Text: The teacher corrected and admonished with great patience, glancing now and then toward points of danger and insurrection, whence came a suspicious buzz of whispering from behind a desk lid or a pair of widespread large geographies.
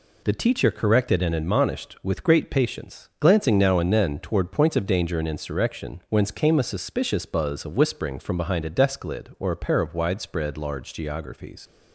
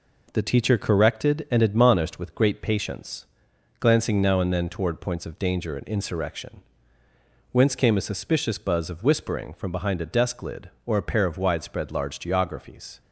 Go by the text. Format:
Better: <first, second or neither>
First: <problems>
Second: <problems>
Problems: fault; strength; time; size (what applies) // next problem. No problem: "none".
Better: second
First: leaves "geographies" unfinished; at 11.6 s; 85 ms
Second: none